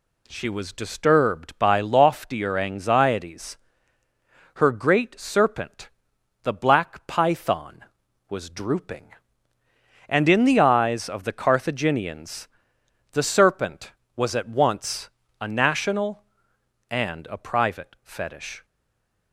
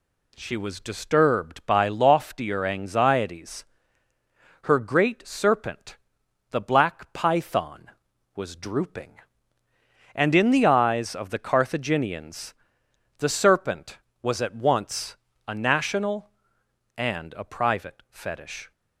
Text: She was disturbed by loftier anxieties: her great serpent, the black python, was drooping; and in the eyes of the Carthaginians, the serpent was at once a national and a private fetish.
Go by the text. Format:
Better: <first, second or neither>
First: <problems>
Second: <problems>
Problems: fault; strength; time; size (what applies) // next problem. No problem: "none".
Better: second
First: pauses between "once" and "a"; slight; at 15.1 s; 0.28 s long // stays silent after the last word; slight; from 18.6 s on; 0.7 s long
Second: pauses between "once" and "a"; slight; at 15.1 s; 0.28 s long